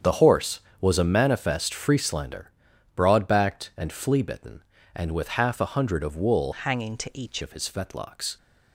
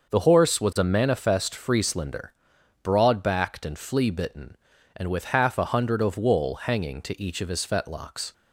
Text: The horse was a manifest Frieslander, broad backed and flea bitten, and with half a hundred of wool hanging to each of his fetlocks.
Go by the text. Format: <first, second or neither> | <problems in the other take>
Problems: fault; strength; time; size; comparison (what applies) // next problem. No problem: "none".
second | starts louder than the rest; strong; until 1.2 s; 8 dB; noticeable in the second // changes voice from "hanging" to "each"; from 6.5 to 7.4 s; 0.9 s long